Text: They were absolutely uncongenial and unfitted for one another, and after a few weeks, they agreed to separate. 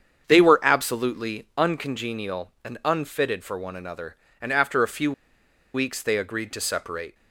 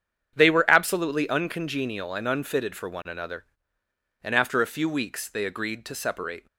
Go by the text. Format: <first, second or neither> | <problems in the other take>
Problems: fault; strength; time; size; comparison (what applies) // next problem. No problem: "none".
second | starts louder than the rest; strong; until 1.2 s; 7.5 dB; strong in the second // pauses between "few" and "weeks"; noticeable; at 5.1 s; 0.61 s long